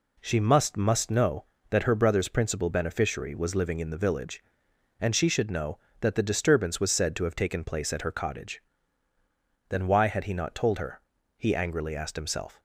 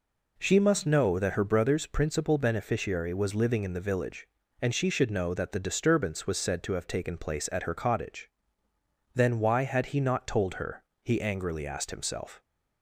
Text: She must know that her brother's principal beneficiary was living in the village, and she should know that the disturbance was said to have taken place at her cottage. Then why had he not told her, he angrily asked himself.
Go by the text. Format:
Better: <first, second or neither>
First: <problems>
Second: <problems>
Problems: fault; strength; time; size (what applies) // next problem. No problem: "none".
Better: second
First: says "must" twice; at 0.7 s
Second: none